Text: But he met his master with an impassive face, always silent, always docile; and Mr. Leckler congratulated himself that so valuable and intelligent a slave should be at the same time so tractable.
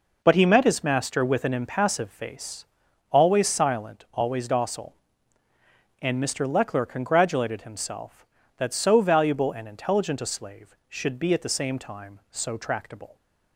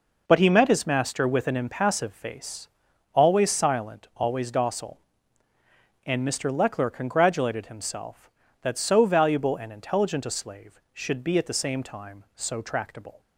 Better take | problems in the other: neither | none

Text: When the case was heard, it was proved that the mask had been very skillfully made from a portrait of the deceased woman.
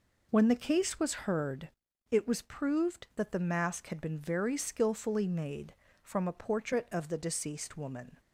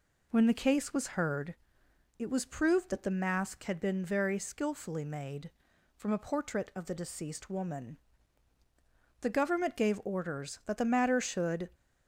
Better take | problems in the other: first | goes on to say "The Government gave orders that the matter should"; strong; from 9.2 s on; 2.4 s long

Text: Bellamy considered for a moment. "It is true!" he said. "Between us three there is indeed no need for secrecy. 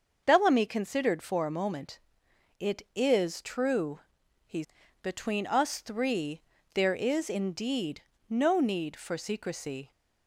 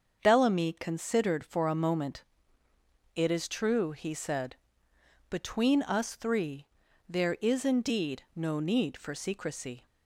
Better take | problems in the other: second | starts louder than the rest; until 1.2 s; 6.5 dB; also in the second // skips "said"; at 4.8 s // pauses between "three" and "there"; slight; at 6.4 s; 0.34 s long; also in the second // pauses between "indeed" and "no"; slight; at 8.0 s; 0.28 s long

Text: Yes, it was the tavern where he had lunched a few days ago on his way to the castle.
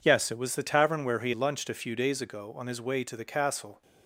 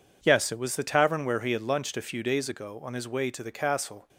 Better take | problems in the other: second | skips "had"; at 1.3 s

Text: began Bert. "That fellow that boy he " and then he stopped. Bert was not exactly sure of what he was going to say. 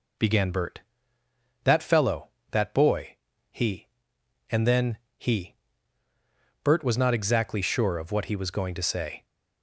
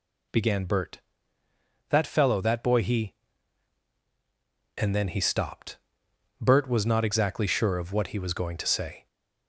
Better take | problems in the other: second | pauses between "boy" and "he"; slight; at 3.1 s; 0.34 s long // pauses between "then" and "he"; slight; at 4.9 s; 0.20 s long // skips "stopped"; at 6.0 s

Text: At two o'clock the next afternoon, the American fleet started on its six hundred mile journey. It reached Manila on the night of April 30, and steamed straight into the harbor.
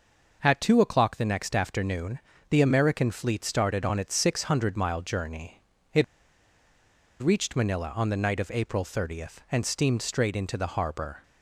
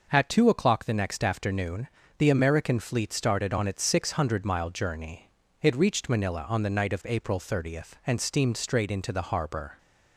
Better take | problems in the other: second | pauses between "It" and "reached"; at 6.0 s; 1.1 s long

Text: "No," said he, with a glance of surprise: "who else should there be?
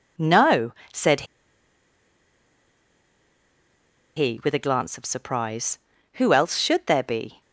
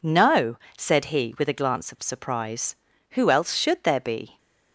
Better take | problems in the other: second | pauses between "said" and "he"; strong; at 1.2 s; 2.9 s long

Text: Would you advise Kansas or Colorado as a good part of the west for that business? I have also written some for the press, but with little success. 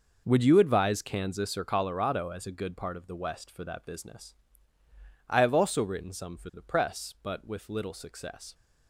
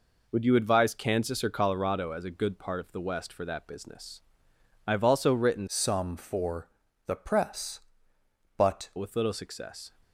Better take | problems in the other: first | changes voice from "some" to "but"; from 5.6 to 8.9 s; 3.3 s long // pauses between "for" and "the"; at 6.6 s; 0.38 s long

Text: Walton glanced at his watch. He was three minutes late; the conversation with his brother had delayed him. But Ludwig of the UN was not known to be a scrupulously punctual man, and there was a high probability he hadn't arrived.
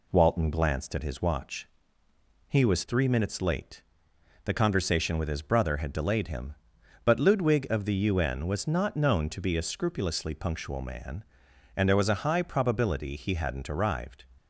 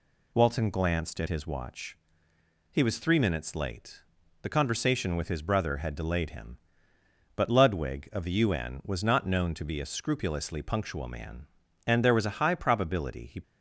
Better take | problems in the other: first | stops before "hadn't arrived"; at 13.4 s

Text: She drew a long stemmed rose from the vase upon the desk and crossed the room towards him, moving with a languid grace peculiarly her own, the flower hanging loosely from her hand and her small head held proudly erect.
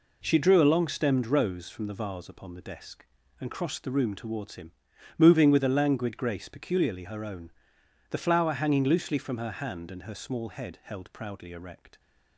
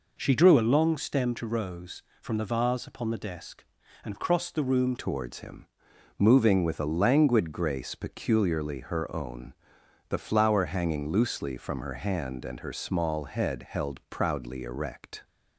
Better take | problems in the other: first | changes voice at "towards"; from 4.9 s on; 10.3 s long

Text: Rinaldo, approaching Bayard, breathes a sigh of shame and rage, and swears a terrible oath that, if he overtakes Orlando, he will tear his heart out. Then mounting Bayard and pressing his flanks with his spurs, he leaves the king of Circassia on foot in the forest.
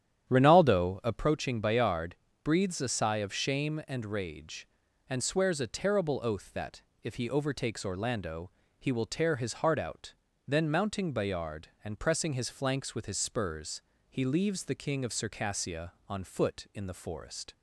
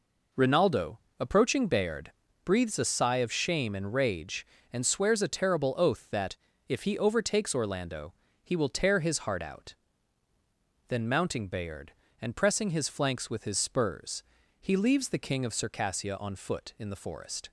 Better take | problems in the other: second | starts louder than the rest; strong; until 1.3 s; 10.5 dB

